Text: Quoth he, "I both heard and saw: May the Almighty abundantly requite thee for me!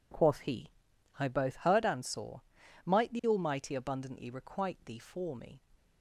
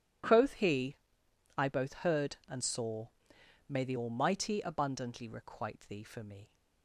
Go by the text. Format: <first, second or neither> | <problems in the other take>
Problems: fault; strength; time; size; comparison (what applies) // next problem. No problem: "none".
second | says "Might" for "May"; at 2.8 s